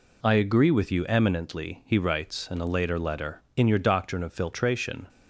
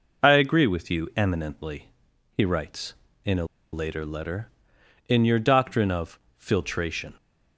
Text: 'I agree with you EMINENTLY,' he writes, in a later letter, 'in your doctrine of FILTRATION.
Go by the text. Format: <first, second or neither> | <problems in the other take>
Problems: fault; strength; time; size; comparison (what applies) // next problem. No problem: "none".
first | pauses between "a" and "later"; slight; at 3.4 s; 0.28 s long // pauses between "of" and "FILTRATION"; slight; at 6.1 s; 0.18 s long